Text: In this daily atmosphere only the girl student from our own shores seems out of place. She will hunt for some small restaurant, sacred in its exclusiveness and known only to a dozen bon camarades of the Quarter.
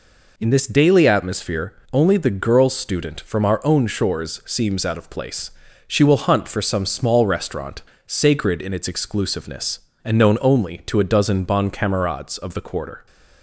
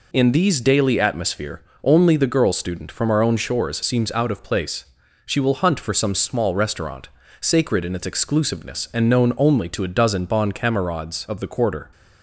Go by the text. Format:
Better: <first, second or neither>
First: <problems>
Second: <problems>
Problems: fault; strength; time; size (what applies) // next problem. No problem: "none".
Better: first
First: pauses between "atmosphere" and "only"; slight; at 1.7 s; 0.22 s long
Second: says "these" for "this"; at 0.3 s // pauses between "atmosphere" and "only"; slight; at 1.6 s; 0.20 s long